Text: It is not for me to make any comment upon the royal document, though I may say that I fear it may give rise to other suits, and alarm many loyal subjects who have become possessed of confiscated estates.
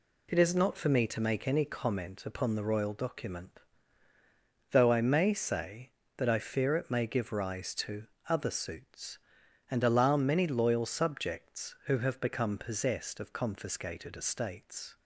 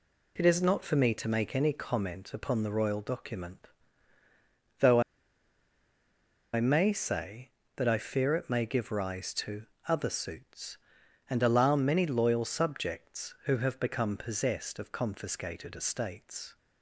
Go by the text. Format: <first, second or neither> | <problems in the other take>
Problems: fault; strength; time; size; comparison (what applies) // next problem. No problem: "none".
first | pauses between "though" and "I"; strong; at 5.0 s; 1.5 s long // pauses between "to" and "other"; slight; at 9.6 s; 0.22 s long; slight in the first